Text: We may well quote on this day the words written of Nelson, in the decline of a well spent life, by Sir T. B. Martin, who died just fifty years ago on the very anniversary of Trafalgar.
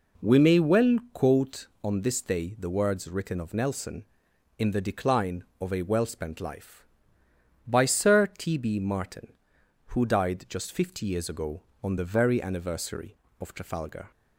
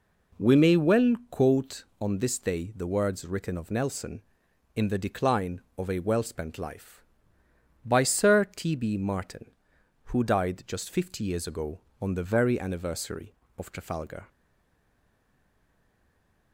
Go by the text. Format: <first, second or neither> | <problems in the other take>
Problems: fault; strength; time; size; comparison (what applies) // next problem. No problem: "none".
first | pauses between "well" and "quote"; slight; at 1.1 s; 0.16 s long; slight in the first // stays silent after the last word; from 14.2 s on; 2.3 s long